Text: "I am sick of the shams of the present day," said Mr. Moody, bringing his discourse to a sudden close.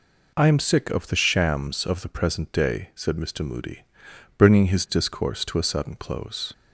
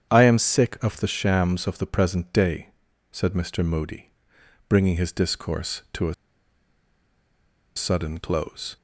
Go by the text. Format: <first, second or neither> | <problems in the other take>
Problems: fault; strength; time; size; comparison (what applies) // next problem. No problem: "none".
first | starts louder than the rest; strong; until 1.1 s; 8.5 dB // pauses between "a" and "sudden"; strong; at 6.1 s; 1.6 s long